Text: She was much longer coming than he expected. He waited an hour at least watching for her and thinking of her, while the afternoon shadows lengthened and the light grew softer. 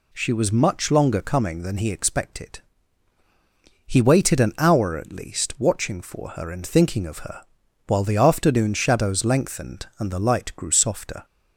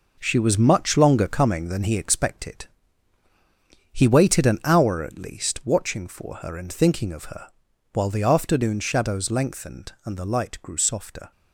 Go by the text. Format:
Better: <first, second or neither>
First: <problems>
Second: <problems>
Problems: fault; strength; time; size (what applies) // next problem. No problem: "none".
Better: first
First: none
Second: gets quieter; strong; throughout; 7 dB